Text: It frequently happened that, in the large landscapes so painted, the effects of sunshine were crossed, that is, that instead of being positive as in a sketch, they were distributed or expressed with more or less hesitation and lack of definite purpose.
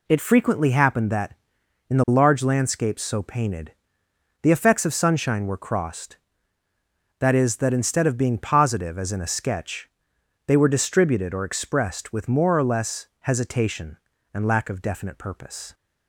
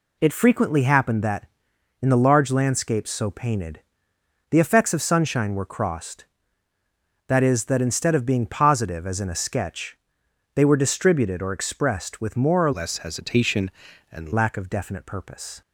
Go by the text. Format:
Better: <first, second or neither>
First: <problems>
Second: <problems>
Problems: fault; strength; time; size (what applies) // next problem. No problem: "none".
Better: first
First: none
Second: changes voice from "less" to "and"; from 12.7 to 14.3 s; 1.6 s long